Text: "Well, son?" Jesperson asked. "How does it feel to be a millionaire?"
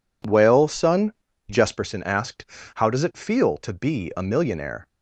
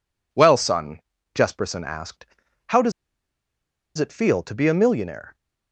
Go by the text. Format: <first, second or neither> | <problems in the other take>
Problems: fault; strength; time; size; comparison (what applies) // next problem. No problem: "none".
first | pauses between "does" and "it"; at 2.9 s; 1.0 s long